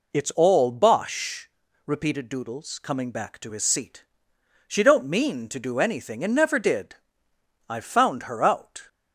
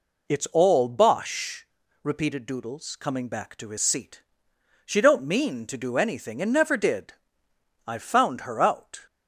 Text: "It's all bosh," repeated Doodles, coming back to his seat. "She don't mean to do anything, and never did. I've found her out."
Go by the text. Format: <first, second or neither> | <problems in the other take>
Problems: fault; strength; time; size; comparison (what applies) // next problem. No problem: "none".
neither | none